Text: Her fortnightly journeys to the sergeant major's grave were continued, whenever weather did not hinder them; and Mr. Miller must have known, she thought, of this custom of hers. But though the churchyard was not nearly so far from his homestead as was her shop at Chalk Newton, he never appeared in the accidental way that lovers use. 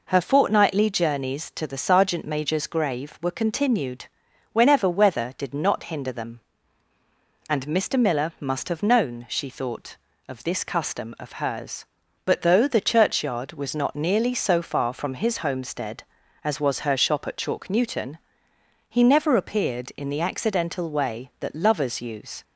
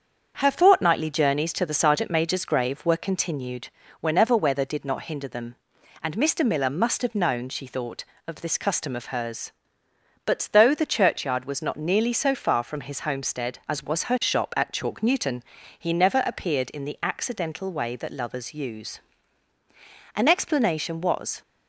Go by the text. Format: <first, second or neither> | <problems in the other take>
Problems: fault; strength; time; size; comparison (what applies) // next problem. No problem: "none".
first | starts louder than the rest; until 1.4 s; 7 dB // goes on to say "An explanation was"; noticeable; from 20.1 s on; 1.2 s long